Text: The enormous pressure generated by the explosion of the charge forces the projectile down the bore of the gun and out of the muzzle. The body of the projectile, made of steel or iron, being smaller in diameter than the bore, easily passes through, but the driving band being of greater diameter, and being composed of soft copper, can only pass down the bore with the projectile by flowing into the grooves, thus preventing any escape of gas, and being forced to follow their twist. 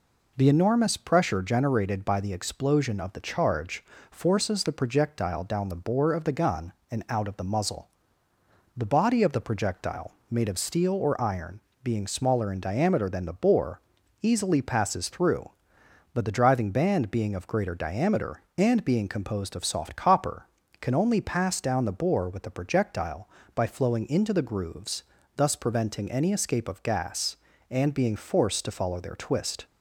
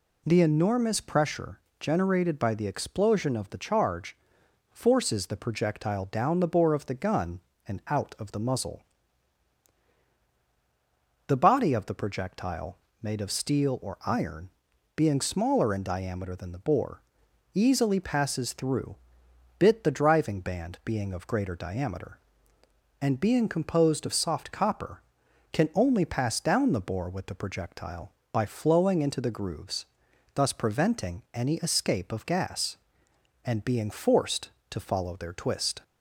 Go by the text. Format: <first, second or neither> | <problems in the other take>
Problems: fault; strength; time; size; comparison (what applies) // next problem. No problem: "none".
first | pauses between "pressure" and "generated"; slight; at 1.5 s; 0.22 s long // pauses between "charge" and "forces"; noticeable; at 4.1 s; 0.56 s long; slight in the first // says "bit" for "but"; at 19.5 s